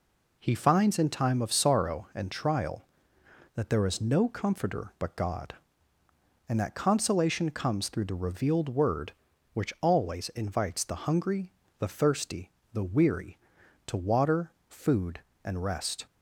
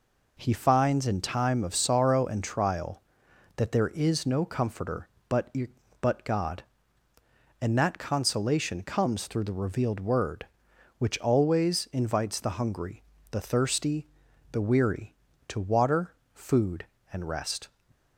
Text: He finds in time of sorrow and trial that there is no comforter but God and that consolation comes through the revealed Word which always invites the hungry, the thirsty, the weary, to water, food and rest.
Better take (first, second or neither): first